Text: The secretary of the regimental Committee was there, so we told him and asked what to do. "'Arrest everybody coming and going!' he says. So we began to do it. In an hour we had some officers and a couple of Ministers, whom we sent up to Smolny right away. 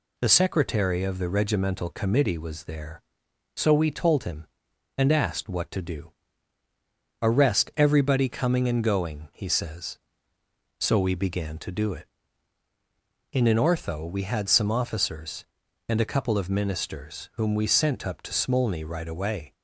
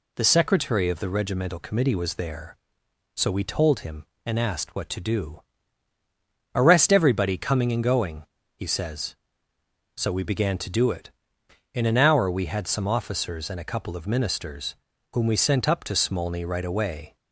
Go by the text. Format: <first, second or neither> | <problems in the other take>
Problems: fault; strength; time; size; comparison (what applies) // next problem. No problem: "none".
second | says "ortho" for "hour"; at 13.5 s